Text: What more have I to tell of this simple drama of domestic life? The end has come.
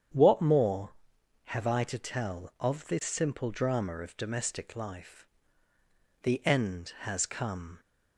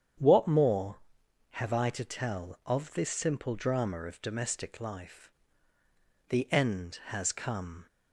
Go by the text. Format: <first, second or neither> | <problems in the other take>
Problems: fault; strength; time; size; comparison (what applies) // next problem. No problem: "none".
neither | starts louder than the rest; strong; the same in both